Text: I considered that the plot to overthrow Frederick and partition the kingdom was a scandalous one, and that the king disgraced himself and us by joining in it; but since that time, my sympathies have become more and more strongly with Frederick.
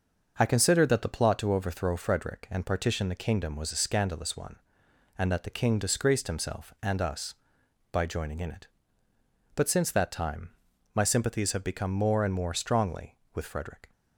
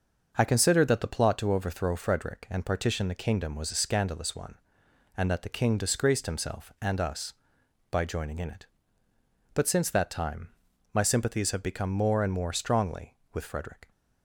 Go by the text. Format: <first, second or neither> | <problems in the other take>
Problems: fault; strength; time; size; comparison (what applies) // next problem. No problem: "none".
neither | starts louder than the rest; the same in both